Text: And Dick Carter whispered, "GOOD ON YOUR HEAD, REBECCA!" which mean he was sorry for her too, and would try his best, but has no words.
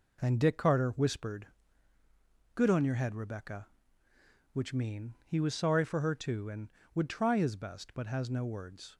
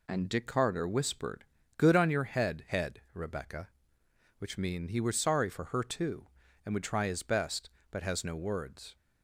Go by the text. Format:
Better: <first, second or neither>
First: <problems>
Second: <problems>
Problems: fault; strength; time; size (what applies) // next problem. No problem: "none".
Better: first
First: none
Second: says "HEAD" twice; at 2.6 s